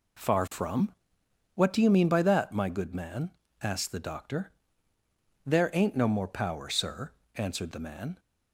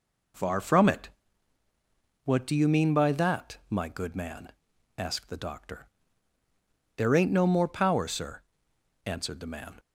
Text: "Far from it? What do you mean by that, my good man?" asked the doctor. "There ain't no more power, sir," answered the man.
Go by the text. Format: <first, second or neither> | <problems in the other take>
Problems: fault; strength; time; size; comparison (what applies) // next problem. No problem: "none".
second | skips "it"; at 1.2 s